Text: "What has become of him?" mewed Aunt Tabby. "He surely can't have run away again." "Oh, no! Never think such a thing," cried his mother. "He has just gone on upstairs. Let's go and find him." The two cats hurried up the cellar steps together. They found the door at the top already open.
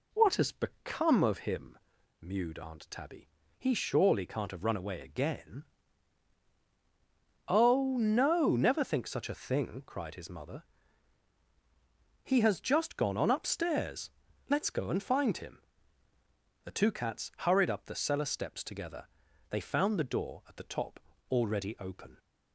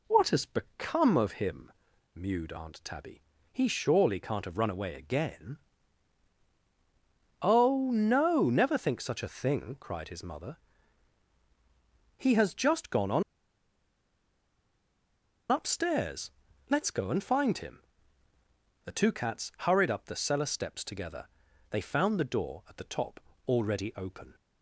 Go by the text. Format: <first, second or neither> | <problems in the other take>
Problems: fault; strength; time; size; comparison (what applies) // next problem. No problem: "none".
first | pauses between "on" and "upstairs"; strong; at 13.2 s; 2.2 s long // pauses between "top" and "already"; slight; at 23.1 s; 0.26 s long; slight in the first